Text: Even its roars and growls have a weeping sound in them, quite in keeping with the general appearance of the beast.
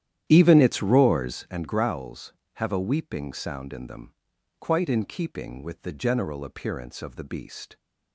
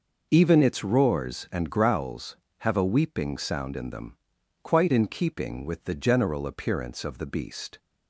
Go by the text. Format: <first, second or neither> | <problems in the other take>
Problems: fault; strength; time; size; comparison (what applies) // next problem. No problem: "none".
second | starts louder than the rest; strong; until 1.5 s; 11 dB